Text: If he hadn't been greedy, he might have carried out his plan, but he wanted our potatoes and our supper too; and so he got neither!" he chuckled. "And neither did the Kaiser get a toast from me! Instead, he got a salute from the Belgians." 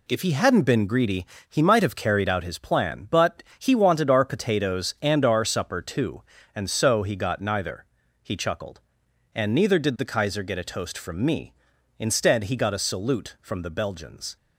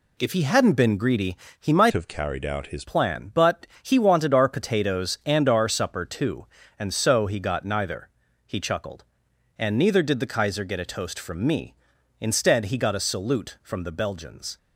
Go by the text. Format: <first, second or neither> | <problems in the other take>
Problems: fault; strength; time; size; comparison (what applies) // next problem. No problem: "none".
first | changes voice from "have" to "his"; from 1.9 to 2.8 s; 0.9 s long // pauses between "but" and "he"; slight; at 3.6 s; 0.16 s long; slight in the first